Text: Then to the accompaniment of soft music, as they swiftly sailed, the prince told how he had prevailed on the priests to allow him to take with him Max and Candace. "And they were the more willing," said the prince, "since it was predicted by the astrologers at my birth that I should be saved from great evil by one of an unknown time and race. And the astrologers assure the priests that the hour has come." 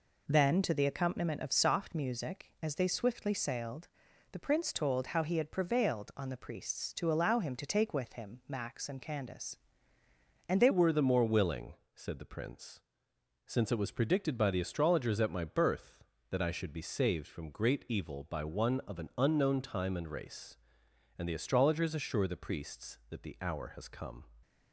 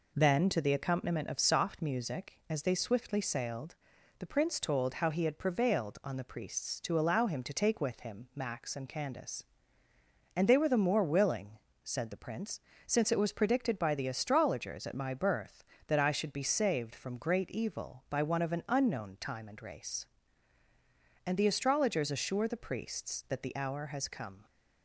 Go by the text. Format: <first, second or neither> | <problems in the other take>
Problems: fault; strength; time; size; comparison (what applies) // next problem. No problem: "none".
second | changes voice at "were"; from 10.7 s on; 13.5 s long